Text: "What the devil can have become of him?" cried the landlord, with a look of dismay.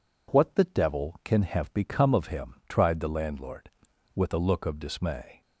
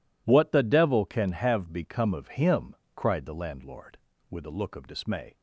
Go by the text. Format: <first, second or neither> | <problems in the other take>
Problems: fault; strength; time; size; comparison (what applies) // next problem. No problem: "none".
second | says "tried" for "cried"; at 2.6 s